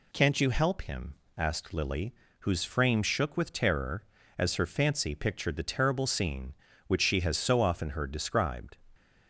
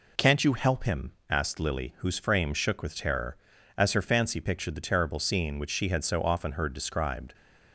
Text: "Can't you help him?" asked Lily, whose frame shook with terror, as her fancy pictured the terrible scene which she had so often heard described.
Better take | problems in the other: second | says "has" for "had"; at 7.2 s

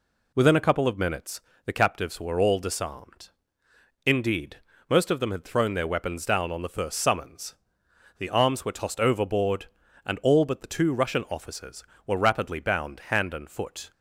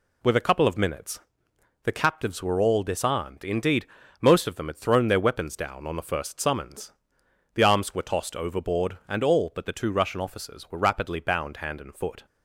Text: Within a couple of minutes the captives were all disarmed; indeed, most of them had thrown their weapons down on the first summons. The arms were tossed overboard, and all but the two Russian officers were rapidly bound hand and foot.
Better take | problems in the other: first | says "With" for "Within"; at 0.2 s // pauses between "minutes" and "the"; noticeable; at 1.1 s; 0.64 s long; slight in the first

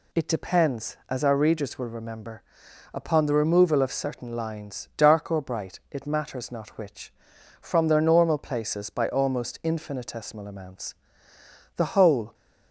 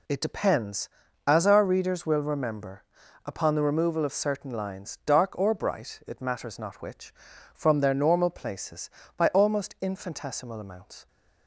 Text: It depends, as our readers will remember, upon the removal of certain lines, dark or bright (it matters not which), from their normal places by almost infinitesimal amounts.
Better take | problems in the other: second | goes on to say "The whole"; from 11.7 s on; 0.56 s long

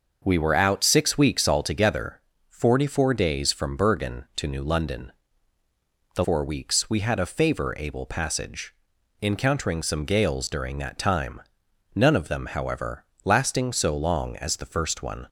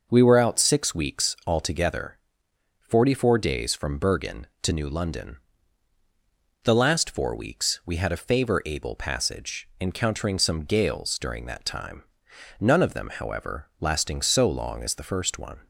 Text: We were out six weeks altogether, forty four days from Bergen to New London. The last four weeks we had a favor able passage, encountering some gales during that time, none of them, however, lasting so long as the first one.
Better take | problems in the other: second | starts louder than the rest; noticeable; until 1.2 s; 6 dB // skips "last"; at 6.2 s

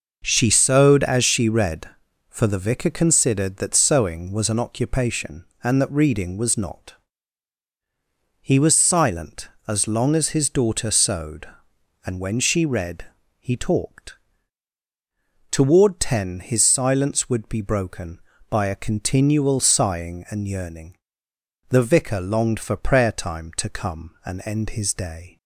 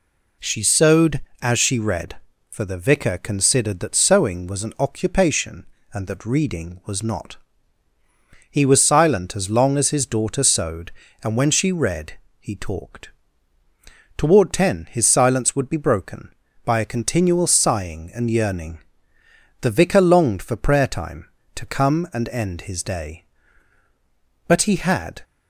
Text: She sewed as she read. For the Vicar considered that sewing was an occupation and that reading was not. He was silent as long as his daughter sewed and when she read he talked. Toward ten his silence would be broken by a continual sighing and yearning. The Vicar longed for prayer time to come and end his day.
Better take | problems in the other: first | pauses between "read" and "he"; slight; at 12.1 s; 0.26 s long; slight in the first // goes on to say "But he had"; noticeable; from 24.4 s on; 0.74 s long

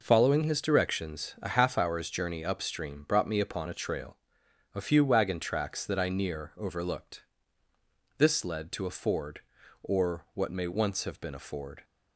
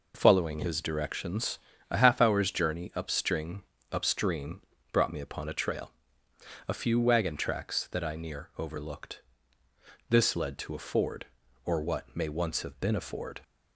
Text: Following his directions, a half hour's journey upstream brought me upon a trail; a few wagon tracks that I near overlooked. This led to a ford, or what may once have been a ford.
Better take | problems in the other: first | says "upstream" twice; at 3.9 s

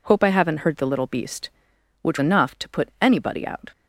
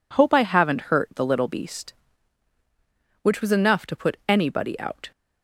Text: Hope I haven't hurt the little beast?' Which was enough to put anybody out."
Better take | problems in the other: second | skips "was"; at 2.1 s

